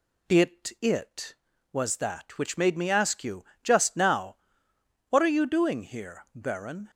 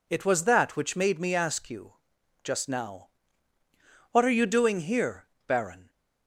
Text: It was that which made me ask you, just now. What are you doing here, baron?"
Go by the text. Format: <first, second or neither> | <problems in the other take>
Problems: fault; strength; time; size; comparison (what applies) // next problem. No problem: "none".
second | says "It" twice; at 0.8 s